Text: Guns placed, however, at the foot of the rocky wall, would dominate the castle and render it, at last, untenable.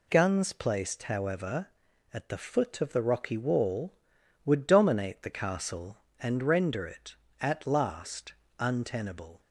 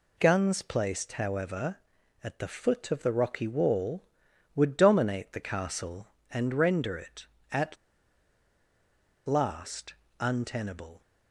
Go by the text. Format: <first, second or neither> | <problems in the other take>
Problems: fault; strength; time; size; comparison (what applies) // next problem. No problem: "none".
first | pauses between "at" and "last"; strong; at 7.7 s; 1.5 s long